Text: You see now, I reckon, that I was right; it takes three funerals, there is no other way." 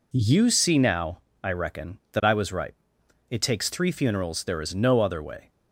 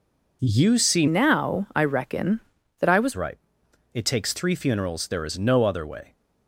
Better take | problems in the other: first | changes voice from "now" to "was"; from 1.0 to 3.1 s; 2.1 s long

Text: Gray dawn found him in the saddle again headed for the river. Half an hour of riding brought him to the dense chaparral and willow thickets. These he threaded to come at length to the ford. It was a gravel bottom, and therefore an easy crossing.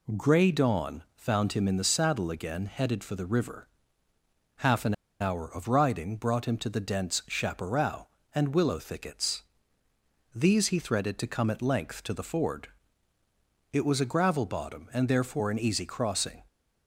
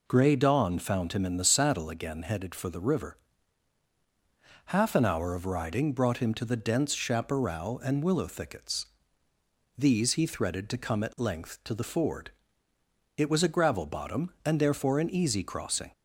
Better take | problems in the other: second | pauses between "an" and "hour"; slight; at 4.9 s; 0.27 s long

